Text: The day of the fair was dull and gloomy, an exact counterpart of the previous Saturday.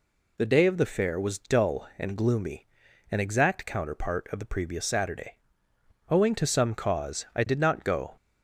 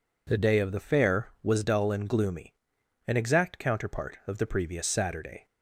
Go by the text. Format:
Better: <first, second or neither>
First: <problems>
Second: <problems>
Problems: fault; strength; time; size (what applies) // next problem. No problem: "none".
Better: second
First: goes on to say "Owing to some cause I did not go"; strong; from 6.0 s on; 2.0 s long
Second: none